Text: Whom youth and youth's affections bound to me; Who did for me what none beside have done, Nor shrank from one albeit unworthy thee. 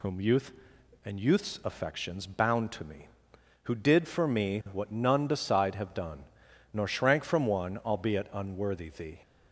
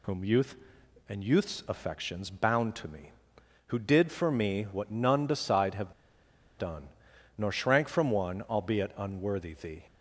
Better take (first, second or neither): first